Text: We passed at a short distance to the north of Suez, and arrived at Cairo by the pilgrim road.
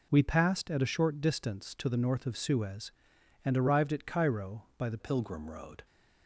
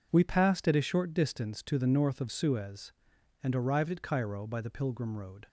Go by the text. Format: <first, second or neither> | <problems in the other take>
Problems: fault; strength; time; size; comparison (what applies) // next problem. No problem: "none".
second | changes voice at "pilgrim"; from 4.9 s on; 0.9 s long